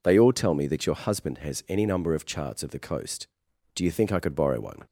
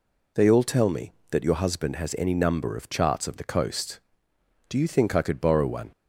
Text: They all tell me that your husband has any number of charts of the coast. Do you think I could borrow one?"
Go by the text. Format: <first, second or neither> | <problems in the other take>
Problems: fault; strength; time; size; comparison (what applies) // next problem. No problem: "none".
neither | none